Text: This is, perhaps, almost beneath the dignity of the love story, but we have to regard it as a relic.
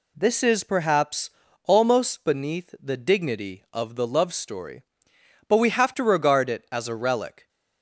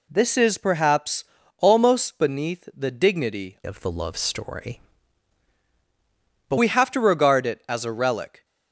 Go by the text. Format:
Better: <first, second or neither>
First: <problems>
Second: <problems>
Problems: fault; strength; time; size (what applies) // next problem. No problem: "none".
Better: first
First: none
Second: changes voice from "of" to "but"; from 3.6 to 6.5 s; 2.9 s long